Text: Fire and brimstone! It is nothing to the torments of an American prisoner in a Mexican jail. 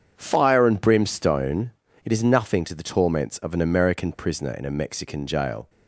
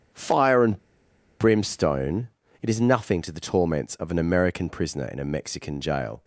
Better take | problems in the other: first | starts louder than the rest; strong; until 1.7 s; 8 dB; strong in the first // pauses between "and" and "brimstone"; noticeable; at 0.7 s; 0.62 s long

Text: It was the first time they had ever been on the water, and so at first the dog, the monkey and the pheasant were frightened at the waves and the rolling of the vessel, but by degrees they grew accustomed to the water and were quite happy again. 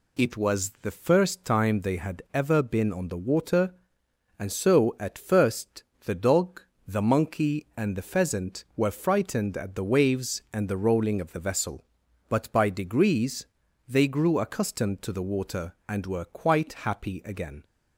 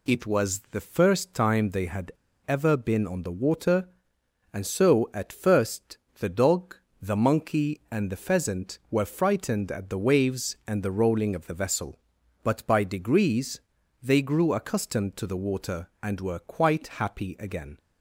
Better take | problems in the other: first | pauses between "had" and "ever"; slight; at 2.1 s; 0.34 s long // pauses between "first" and "the"; slight; at 5.9 s; 0.20 s long; slight in the first // pauses between "degrees" and "they"; at 13.5 s; 0.42 s long; also in the first

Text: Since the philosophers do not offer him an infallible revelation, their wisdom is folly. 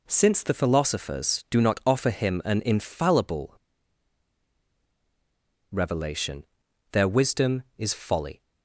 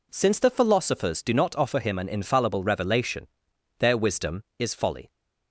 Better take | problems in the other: second | pauses between "infallible" and "revelation"; strong; at 3.5 s; 2.1 s long

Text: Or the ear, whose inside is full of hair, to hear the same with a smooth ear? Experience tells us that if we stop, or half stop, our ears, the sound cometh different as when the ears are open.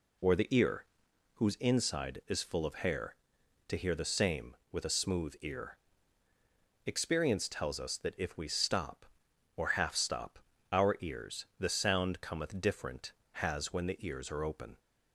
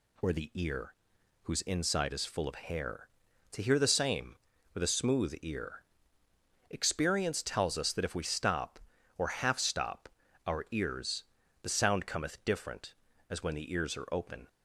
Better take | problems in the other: second | says "has" for "as"; at 13.3 s

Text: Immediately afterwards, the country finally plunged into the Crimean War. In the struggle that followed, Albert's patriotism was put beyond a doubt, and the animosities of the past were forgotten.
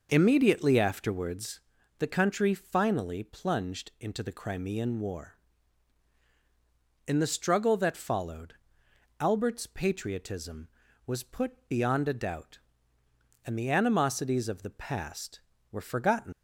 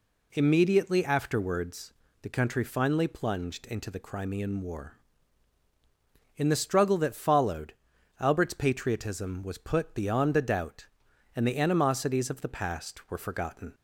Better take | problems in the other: second | leaves "forgotten" unfinished; at 16.3 s; 95 ms

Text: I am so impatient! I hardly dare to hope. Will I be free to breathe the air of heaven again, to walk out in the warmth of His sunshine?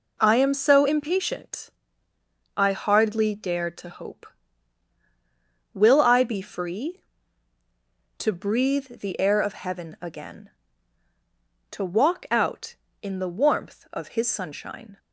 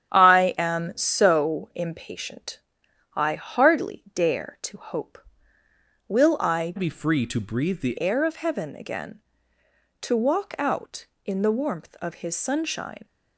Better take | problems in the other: first | starts louder than the rest; strong; until 1.1 s; 9.5 dB // changes voice from "be" to "the"; from 6.7 to 7.9 s; 1.2 s long

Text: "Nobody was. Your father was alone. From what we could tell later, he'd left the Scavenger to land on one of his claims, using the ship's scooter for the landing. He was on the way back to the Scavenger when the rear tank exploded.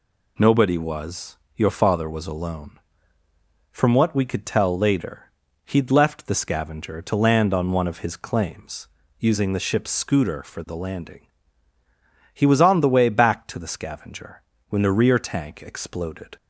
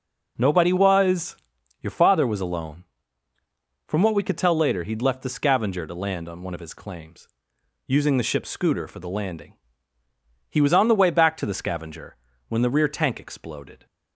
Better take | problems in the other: neither | pauses between "Scavenger" and "when"; slight; the same in both

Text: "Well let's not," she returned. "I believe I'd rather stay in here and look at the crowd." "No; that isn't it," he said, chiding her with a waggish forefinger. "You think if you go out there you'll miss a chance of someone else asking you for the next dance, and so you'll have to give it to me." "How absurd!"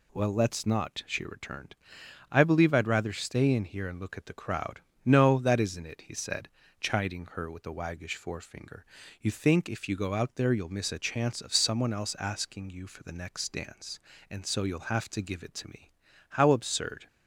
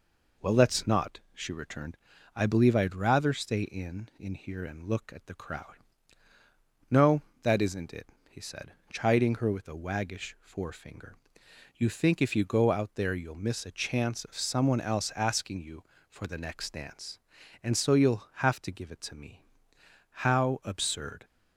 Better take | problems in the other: first | says "in" twice; at 4.2 s

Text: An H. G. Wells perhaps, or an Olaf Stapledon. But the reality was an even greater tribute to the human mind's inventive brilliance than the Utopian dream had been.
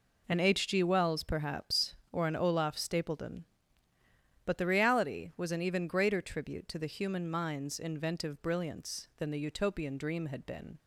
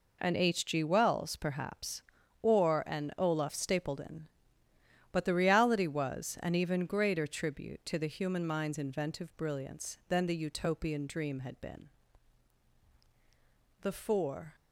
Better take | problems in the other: first | goes on to say "The four"; noticeable; from 13.8 s on; 0.74 s long

